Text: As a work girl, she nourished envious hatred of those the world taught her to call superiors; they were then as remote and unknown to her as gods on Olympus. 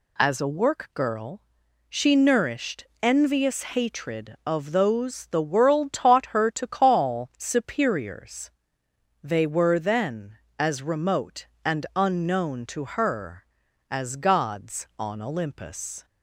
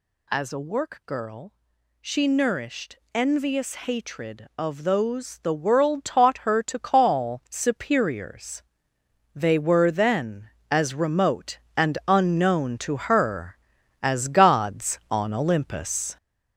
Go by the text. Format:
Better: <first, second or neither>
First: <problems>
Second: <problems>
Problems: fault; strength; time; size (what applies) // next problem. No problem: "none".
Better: first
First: pauses between "nourished" and "envious"; slight; at 2.8 s; 0.18 s long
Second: gets louder; noticeable; throughout; 5.5 dB // pauses between "nourished" and "envious"; slight; at 2.9 s; 0.18 s long